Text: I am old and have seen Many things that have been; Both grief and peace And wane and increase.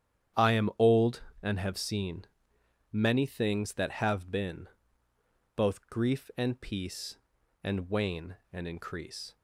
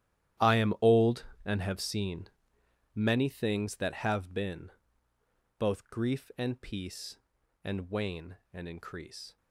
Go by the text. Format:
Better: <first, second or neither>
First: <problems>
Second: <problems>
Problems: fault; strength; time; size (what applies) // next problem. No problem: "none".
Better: first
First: starts louder than the rest; strong; until 1.7 s; 9.5 dB // pauses between "seen" and "Many"; noticeable; at 2.2 s; 0.70 s long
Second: gets quieter; strong; throughout; 16 dB // starts louder than the rest; strong; until 1.7 s; 12 dB // pauses between "seen" and "Many"; noticeable; at 2.2 s; 0.70 s long